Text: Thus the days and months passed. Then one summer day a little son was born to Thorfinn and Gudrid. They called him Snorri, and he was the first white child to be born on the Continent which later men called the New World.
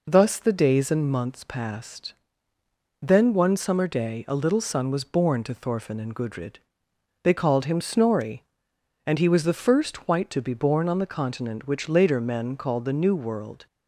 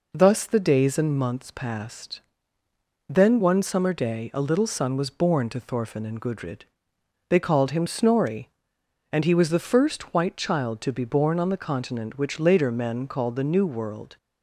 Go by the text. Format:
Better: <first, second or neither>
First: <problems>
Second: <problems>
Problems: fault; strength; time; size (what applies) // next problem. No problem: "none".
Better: second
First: skips "child"; at 10.3 s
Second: none